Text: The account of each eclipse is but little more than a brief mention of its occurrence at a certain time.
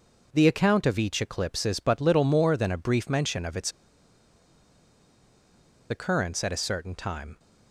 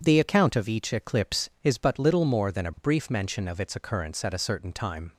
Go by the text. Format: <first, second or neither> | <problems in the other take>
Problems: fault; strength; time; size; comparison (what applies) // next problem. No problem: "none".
second | pauses between "its" and "occurrence"; strong; at 3.7 s; 2.1 s long